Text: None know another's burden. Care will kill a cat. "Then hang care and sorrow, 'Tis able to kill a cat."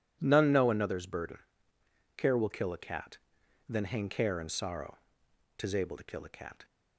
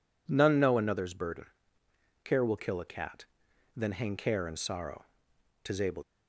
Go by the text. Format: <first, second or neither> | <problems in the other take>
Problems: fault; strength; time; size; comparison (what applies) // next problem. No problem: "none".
first | stops before "to kill a cat"; at 6.0 s